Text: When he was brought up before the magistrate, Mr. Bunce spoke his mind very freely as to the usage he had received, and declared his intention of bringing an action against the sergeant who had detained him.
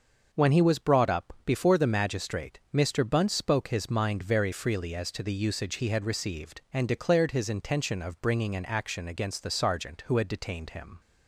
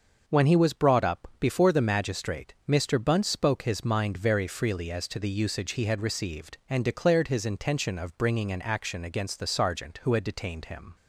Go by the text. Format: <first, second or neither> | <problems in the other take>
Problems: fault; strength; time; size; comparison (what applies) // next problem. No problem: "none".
neither | starts louder than the rest; the same in both